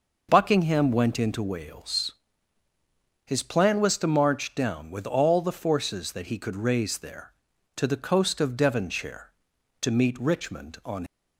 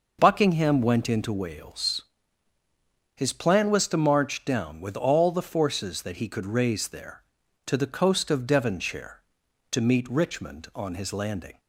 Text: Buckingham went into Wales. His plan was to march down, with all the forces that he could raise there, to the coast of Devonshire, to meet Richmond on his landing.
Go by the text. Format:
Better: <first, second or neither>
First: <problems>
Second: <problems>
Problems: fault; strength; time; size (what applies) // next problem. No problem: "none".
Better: second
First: stops before "his landing"; at 11.0 s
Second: none